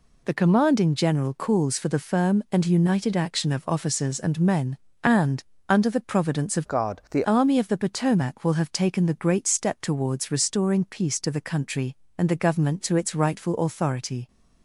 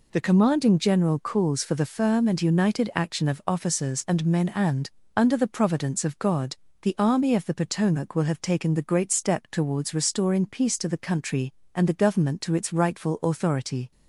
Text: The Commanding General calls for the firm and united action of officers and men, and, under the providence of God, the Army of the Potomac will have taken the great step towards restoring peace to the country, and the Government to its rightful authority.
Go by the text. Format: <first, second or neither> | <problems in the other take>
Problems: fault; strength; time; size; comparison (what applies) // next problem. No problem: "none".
second | changes voice from "God" to "the"; from 6.6 to 7.2 s; 0.6 s long